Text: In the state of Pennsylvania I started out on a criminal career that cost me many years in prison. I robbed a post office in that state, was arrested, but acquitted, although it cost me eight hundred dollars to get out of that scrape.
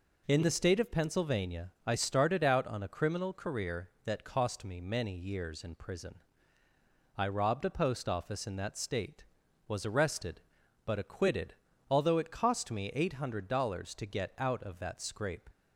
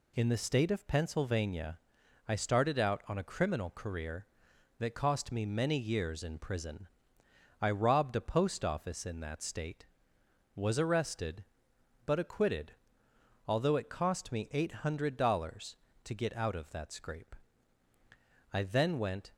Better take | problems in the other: first | pauses between "Pennsylvania" and "I"; noticeable; at 1.7 s; 0.50 s long // goes on to say "I then went"; noticeable; from 18.5 s on; 0.80 s long

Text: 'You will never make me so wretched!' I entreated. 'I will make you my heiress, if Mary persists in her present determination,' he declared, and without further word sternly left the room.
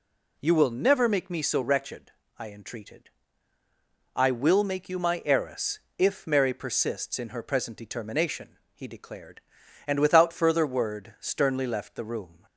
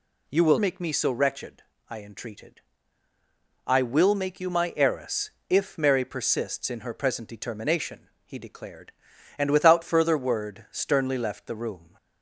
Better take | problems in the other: first | skips "never"; at 0.5 s

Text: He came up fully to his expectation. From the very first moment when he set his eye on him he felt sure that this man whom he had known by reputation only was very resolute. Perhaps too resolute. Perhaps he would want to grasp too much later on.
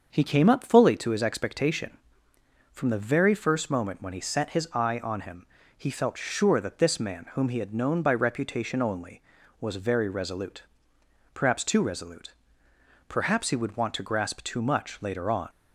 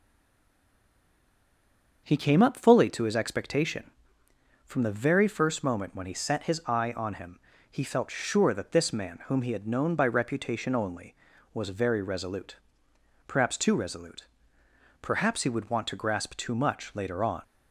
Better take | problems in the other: first | stays silent before the first word; noticeable; until 2.0 s; 2.0 s long // starts louder than the rest; until 3.0 s; 6.5 dB; also in the first // pauses between "him" and "he"; slight; at 7.3 s; 0.32 s long; slight in the first

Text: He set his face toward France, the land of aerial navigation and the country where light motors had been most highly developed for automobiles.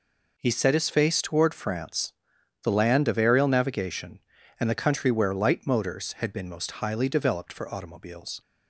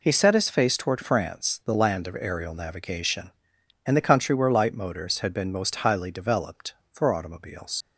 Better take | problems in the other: first | leaves "automobiles" unfinished; at 7.8 s; 75 ms

